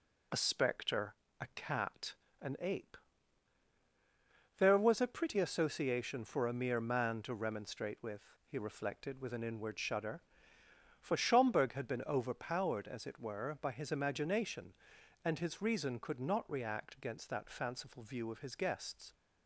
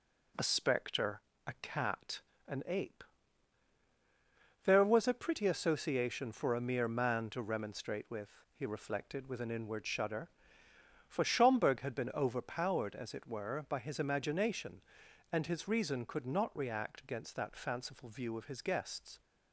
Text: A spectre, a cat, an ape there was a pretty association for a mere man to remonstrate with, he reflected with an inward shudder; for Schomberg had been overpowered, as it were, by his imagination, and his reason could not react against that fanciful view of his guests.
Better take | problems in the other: second | loses the start of "A"; at 0.3 s; 30 ms // pauses between "ape" and "there"; strong; at 2.9 s; 1.6 s long; strong in the second

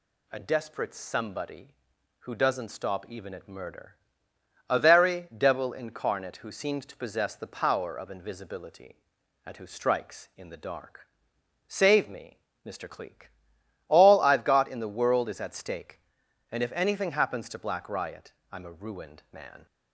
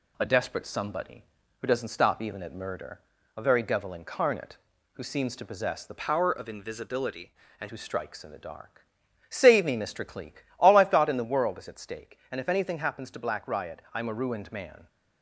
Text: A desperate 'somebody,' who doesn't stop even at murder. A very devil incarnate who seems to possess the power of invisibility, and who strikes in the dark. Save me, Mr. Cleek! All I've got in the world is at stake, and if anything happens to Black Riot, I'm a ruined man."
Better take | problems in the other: first | changes voice from "power" to "and"; from 5.9 to 7.6 s; 1.7 s long

